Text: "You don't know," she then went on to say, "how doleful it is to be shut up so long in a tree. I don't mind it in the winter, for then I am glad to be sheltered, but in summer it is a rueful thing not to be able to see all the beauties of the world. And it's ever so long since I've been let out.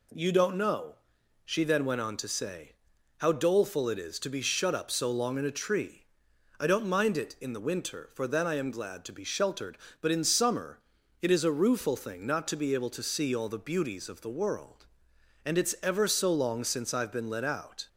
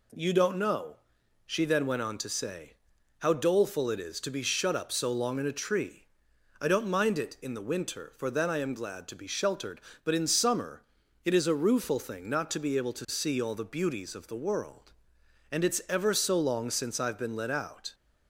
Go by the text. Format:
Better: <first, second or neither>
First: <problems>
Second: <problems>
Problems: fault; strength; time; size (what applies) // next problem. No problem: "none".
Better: neither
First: pauses between "summer" and "it"; at 10.7 s; 0.40 s long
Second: pauses between "summer" and "it"; at 10.8 s; 0.40 s long